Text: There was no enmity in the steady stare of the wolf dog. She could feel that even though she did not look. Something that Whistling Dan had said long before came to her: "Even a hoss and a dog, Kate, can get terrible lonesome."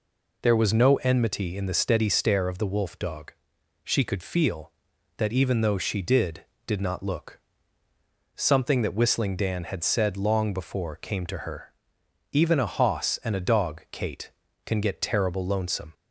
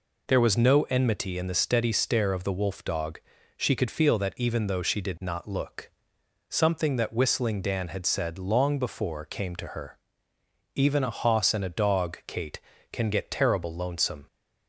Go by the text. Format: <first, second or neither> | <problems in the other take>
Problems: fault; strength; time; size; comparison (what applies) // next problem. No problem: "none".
second | says "did" twice; at 6.6 s